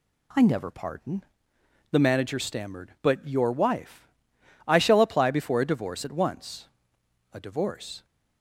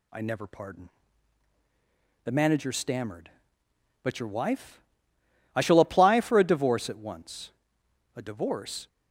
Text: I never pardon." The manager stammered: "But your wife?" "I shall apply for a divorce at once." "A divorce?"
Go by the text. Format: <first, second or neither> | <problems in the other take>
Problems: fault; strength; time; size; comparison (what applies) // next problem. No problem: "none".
second | says "before" for "for"; at 5.2 s